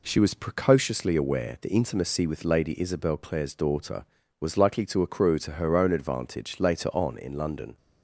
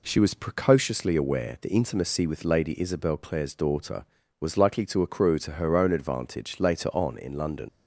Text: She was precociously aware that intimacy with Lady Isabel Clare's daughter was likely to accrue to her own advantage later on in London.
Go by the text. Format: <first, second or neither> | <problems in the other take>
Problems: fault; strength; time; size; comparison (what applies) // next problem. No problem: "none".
first | leaves "London" unfinished; at 7.6 s; 75 ms